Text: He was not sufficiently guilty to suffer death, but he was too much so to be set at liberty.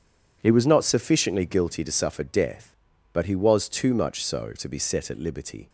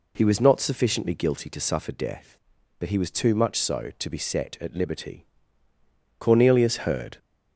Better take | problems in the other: first | goes on to say "Cornelius heard"; noticeable; from 6.2 s on; 0.98 s long

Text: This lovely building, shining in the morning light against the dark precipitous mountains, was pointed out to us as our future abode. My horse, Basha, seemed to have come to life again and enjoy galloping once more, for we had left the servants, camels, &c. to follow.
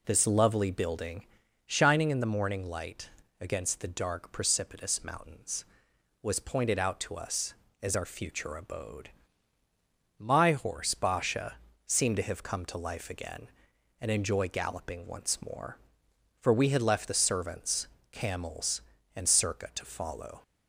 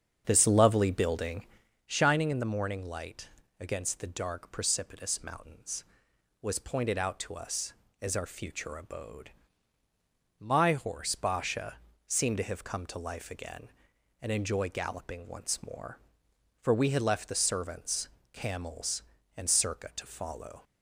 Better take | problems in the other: first | starts louder than the rest; strong; until 1.8 s; 7.5 dB // pauses between "light" and "against"; slight; at 3.2 s; 0.32 s long; slight in the first

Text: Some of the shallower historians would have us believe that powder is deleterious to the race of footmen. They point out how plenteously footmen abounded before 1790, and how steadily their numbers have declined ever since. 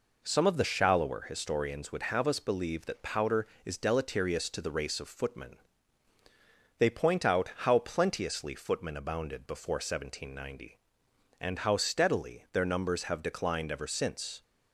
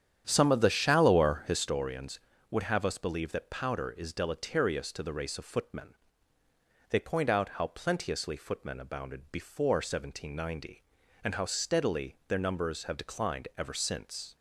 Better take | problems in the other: first | starts louder than the rest; strong; until 1.8 s; 9.5 dB

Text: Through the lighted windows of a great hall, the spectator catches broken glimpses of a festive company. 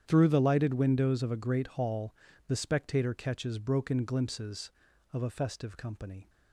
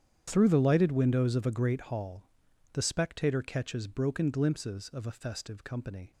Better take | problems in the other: neither | starts louder than the rest; strong; the same in both

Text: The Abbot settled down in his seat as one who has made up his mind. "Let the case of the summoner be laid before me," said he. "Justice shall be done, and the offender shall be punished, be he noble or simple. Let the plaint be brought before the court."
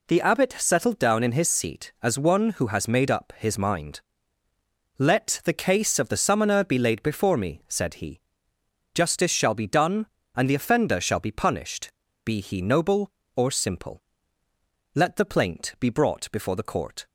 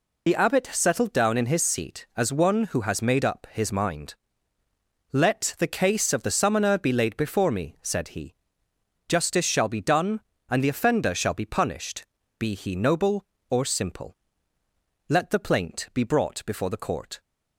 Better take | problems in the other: first | loses the start of "The"; at 0.2 s; 45 ms

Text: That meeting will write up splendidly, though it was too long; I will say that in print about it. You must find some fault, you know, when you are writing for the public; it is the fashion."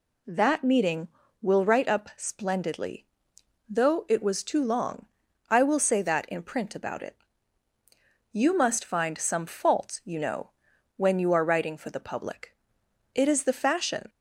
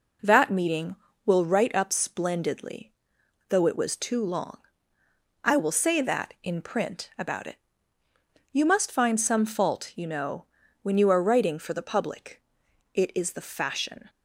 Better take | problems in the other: neither | none

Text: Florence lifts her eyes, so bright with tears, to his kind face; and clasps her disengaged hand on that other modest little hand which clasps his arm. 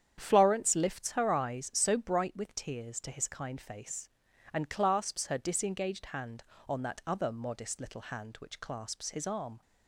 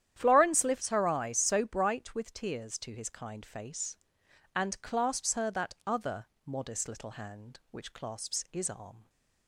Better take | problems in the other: first | starts louder than the rest; strong; until 1.1 s; 10.5 dB; strong in the first // skips "disengaged hand on"; at 5.5 s // pauses between "other" and "modest"; slight; at 6.2 s; 0.18 s long

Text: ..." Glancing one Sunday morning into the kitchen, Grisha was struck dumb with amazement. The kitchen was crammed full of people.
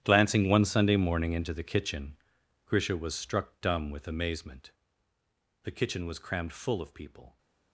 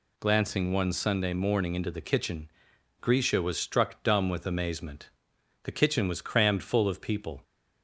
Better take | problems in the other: second | gets quieter; strong; throughout; 18 dB

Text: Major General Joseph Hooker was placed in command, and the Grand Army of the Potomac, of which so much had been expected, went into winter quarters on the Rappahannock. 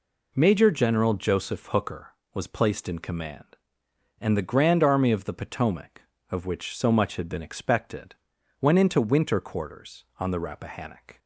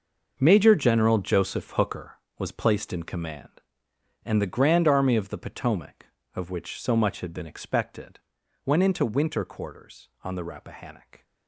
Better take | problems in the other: first | gets quieter; strong; throughout; 13 dB

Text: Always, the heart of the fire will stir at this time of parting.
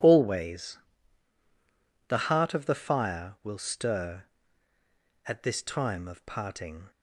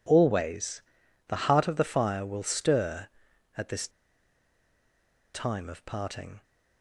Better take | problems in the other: first | pauses between "this" and "time"; strong; at 3.8 s; 1.4 s long

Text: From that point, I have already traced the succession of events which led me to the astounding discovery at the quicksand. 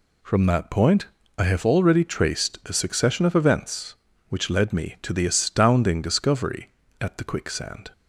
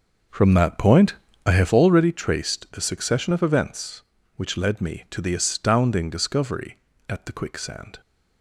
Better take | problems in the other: first | starts louder than the rest; until 2.1 s; 6 dB

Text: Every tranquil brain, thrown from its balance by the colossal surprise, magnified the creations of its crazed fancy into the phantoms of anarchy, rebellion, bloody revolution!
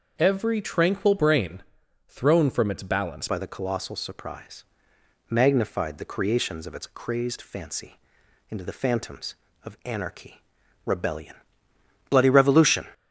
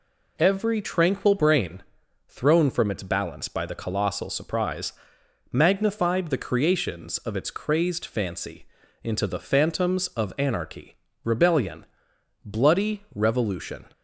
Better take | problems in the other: second | changes voice at "by"; from 3.2 s on; 9.6 s long // pauses between "fancy" and "into"; noticeable; at 7.9 s; 0.52 s long; also in the second

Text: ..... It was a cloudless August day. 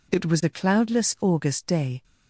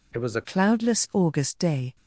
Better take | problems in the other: first | changes voice from "It" to "a"; from 0.1 to 0.4 s; 0.3 s long

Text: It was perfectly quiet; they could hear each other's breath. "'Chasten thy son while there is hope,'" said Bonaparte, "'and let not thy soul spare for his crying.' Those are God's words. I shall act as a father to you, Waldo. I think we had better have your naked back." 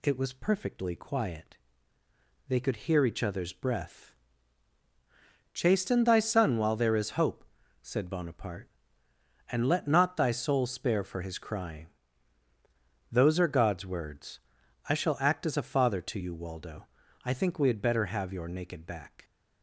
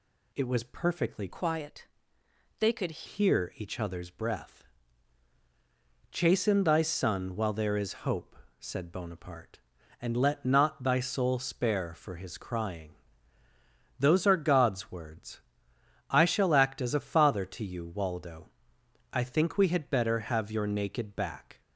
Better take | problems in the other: first | changes voice from "quiet" to "could"; from 1.3 to 3.0 s; 1.7 s long

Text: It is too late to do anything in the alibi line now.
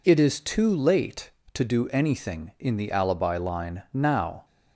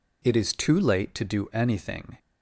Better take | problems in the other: first | stops before "in the alibi line now"; at 2.1 s

